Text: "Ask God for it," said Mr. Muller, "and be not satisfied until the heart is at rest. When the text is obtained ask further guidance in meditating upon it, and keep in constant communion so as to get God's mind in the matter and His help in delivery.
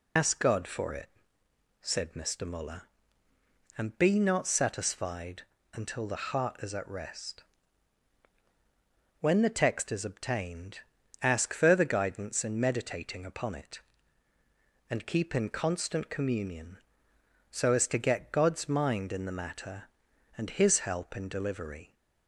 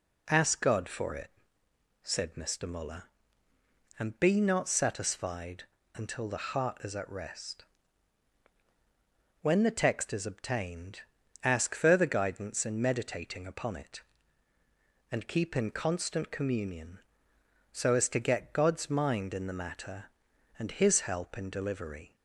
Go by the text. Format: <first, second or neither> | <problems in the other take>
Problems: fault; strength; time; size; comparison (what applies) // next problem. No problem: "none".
second | loses the start of "Ask"; at 0.1 s; 90 ms // pauses between "satisfied" and "until"; slight; at 5.4 s; 0.30 s long; slight in the second // pauses between "obtained" and "ask"; at 10.7 s; 0.42 s long; also in the second